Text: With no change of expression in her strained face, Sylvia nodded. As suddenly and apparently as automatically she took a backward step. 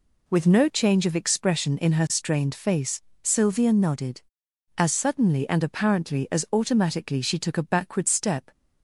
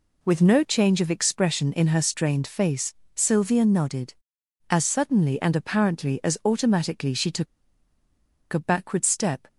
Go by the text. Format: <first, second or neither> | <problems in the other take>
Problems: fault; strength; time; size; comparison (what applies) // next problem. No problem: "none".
first | pauses between "took" and "a"; at 7.4 s; 1.0 s long